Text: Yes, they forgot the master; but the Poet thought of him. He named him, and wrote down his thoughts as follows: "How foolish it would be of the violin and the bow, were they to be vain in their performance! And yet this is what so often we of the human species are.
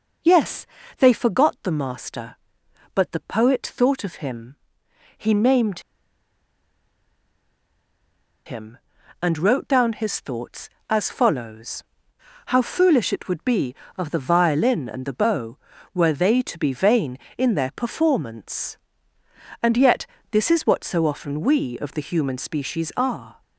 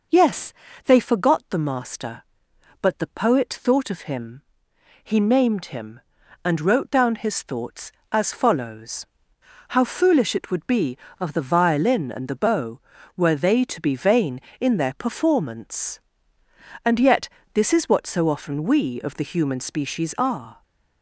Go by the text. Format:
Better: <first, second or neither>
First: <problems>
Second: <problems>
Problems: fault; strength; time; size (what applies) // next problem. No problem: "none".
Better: second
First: pauses between "named" and "him"; strong; at 5.7 s; 2.6 s long // pauses between "yet" and "this"; slight; at 20.0 s; 0.24 s long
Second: pauses between "yet" and "this"; slight; at 17.2 s; 0.24 s long